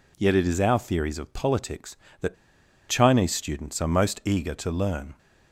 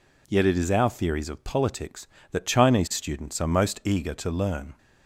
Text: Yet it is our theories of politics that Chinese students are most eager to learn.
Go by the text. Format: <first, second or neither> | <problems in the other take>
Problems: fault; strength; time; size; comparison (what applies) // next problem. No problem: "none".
second | pauses between "that" and "Chinese"; noticeable; at 2.3 s; 0.54 s long